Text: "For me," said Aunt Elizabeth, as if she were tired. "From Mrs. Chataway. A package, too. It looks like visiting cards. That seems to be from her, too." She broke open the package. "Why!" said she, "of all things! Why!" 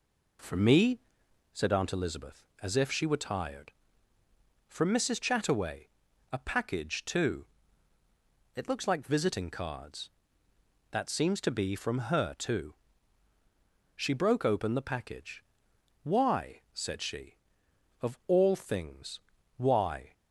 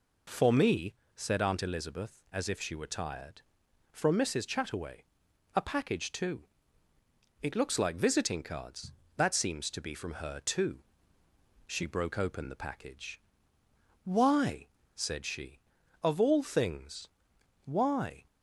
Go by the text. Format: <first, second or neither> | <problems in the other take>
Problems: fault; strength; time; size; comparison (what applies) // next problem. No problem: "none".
neither | none